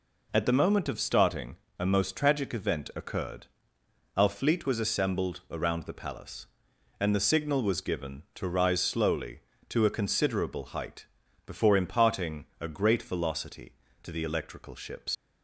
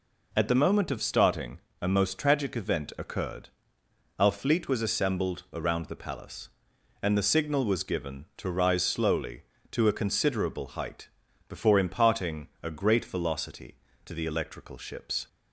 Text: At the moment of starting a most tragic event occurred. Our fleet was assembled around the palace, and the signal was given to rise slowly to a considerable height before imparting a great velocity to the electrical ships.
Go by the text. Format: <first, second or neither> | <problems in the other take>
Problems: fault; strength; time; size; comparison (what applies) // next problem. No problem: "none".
second | pauses between "starting" and "a"; slight; at 1.5 s; 0.24 s long; slight in the second // pauses between "height" and "before"; at 11.0 s; 0.40 s long; also in the second // pauses between "imparting" and "a"; slight; at 12.4 s; 0.16 s long; slight in the second // leaves "ships" unfinished; at 15.1 s; 100 ms